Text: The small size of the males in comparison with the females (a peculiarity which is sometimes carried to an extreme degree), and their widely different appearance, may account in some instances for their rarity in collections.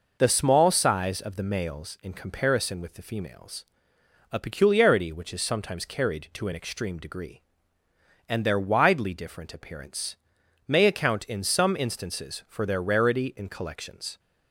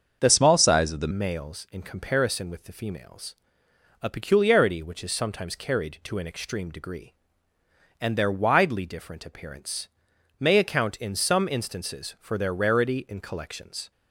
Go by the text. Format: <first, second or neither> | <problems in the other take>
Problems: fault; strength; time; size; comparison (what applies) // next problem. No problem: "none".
first | starts louder than the rest; until 1.2 s; 7 dB // changes voice from "small" to "the"; from 0.2 to 1.1 s; 0.9 s long